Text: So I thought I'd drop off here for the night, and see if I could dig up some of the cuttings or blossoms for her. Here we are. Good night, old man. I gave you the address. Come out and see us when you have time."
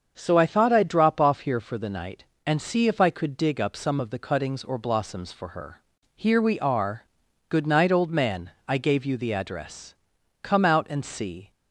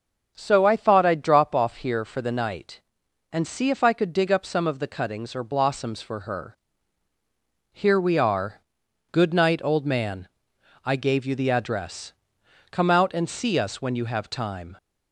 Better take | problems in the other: second | starts louder than the rest; until 1.1 s; 6.5 dB; also in the second // stops before "us when you have time"; at 11.5 s

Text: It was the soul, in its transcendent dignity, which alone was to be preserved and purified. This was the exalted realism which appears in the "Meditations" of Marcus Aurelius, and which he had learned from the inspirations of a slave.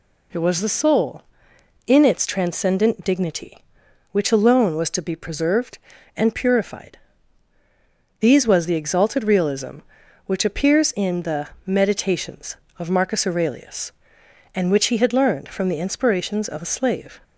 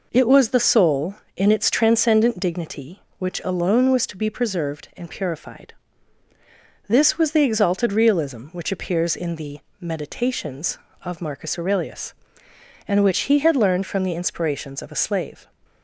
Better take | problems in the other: second | says "These" for "This"; at 8.2 s // pauses between "the" and "Meditations"; slight; at 11.4 s; 0.18 s long; slight in the second

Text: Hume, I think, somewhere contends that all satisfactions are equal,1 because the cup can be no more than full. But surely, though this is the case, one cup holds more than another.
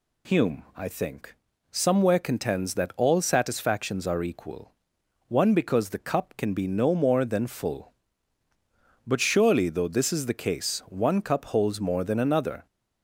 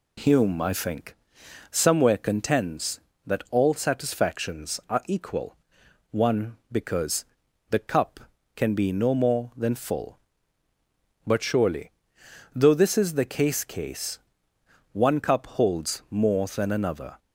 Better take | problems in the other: first | pauses between "because" and "the"; noticeable; at 7.2 s; 0.46 s long // says "case" twice; at 13.6 s

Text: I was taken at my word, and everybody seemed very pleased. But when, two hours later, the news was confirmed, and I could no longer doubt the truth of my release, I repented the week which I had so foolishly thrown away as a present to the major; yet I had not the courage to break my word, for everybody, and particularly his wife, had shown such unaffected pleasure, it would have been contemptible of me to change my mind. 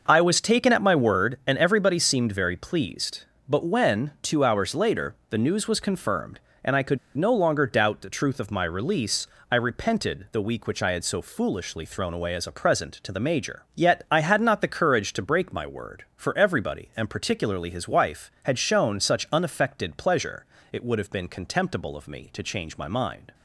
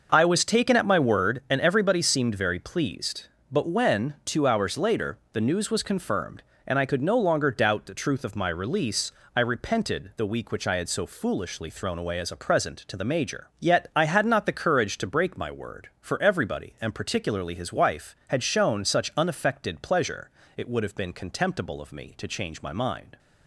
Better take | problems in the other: second | pauses between "could" and "no"; slight; at 6.9 s; 0.19 s long

